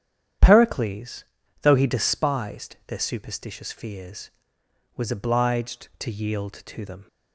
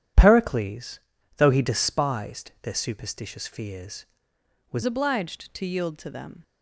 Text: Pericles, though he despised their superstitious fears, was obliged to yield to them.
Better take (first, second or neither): first